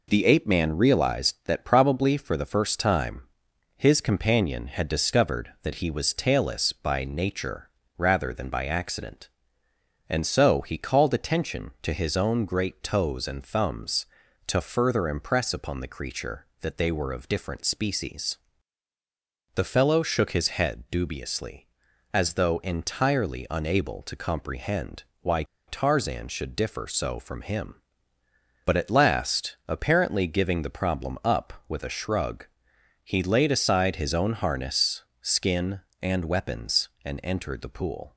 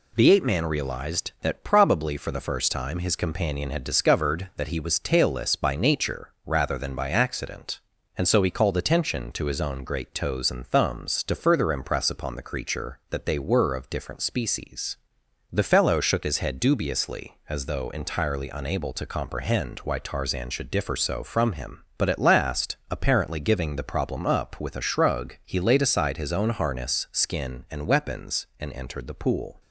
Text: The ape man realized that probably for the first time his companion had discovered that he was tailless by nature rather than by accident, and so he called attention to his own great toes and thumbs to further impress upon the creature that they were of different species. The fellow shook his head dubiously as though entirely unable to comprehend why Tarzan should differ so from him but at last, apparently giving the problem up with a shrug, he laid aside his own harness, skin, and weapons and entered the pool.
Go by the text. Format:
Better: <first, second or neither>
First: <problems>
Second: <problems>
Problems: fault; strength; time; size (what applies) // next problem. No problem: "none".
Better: second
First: pauses between "time" and "his"; noticeable; at 3.2 s; 0.54 s long // pauses between "nature" and "rather"; slight; at 7.6 s; 0.28 s long // pauses between "comprehend" and "why"; slight; at 25.0 s; 0.18 s long // pauses between "why" and "Tarzan"; slight; at 25.4 s; 0.24 s long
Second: pauses between "nature" and "rather"; slight; at 6.3 s; 0.16 s long